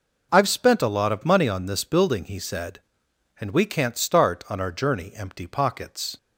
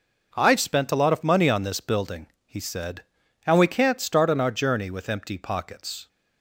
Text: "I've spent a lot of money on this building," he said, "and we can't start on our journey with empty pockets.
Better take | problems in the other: second | skips "with"; at 5.1 s

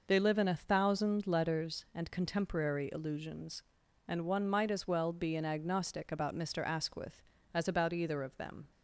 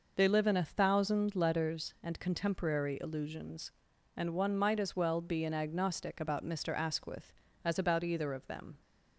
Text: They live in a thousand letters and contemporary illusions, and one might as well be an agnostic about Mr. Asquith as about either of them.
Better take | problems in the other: neither | none

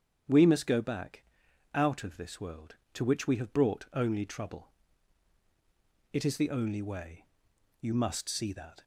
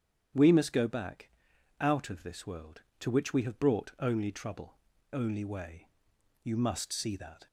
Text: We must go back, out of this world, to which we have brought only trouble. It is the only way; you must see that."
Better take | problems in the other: first | starts louder than the rest; strong; until 1.8 s; 8.5 dB; strong in the first // skips "It is the"; at 4.9 s

